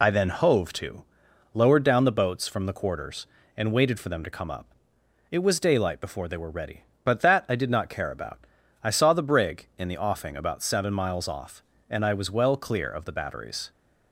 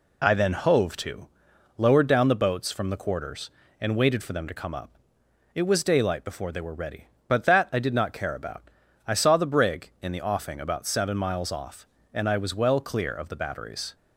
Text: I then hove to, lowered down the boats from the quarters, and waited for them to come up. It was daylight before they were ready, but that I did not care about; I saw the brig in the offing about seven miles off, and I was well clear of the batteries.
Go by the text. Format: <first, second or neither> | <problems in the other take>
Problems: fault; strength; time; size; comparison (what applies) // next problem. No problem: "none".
second | loses the start of "I"; at 0.0 s; 25 ms